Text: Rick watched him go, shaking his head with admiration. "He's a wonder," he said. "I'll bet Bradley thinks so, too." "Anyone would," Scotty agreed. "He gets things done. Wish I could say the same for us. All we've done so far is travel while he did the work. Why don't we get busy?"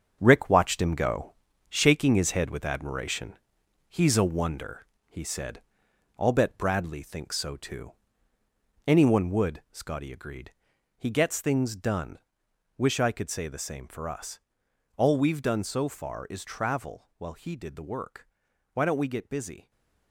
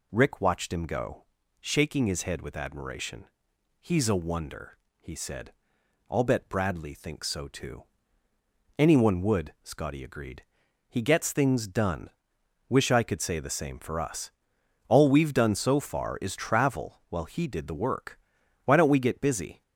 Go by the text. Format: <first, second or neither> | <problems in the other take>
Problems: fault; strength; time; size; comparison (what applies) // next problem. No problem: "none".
second | gets quieter; strong; throughout; 9 dB // stays silent after the last word; slight; from 19.6 s on; 0.5 s long